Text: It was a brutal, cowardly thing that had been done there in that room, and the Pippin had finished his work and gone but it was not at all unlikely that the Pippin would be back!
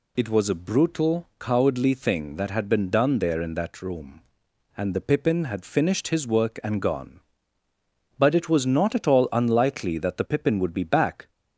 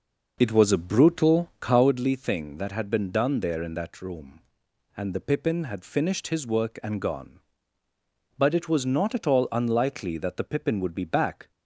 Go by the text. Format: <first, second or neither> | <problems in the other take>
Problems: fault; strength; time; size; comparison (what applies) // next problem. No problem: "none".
first | starts louder than the rest; noticeable; until 1.9 s; 5.5 dB